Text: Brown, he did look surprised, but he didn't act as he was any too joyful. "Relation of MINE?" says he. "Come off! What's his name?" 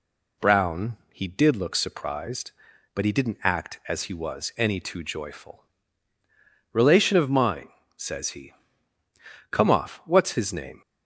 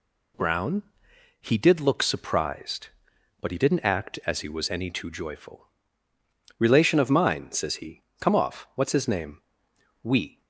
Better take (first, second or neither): first